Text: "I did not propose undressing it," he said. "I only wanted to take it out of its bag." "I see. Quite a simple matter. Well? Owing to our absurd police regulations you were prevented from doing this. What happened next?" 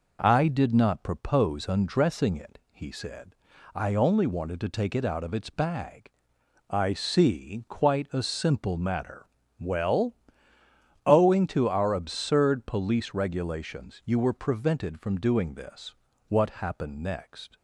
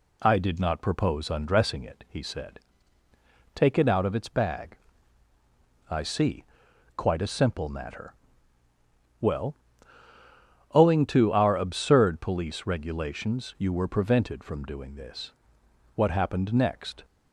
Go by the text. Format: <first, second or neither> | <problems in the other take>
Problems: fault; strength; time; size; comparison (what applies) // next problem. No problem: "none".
first | skips "I only wanted to"; at 3.0 s